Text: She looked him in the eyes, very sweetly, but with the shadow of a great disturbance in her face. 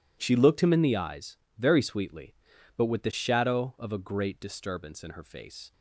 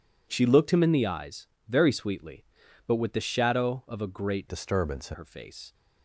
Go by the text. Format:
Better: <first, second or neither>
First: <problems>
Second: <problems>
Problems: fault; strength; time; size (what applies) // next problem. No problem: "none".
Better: first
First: none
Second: changes voice from "disturbance" to "in"; from 4.4 to 5.1 s; 0.7 s long